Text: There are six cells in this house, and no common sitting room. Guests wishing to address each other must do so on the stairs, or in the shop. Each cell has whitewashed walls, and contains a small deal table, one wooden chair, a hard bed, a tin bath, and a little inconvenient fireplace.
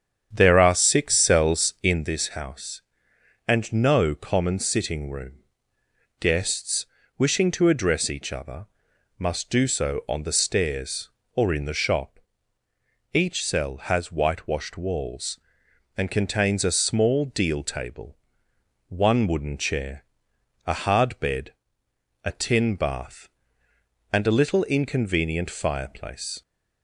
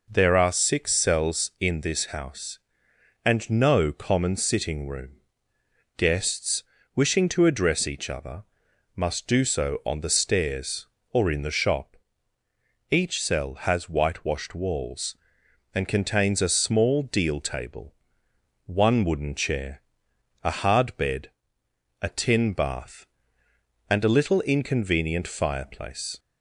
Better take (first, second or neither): second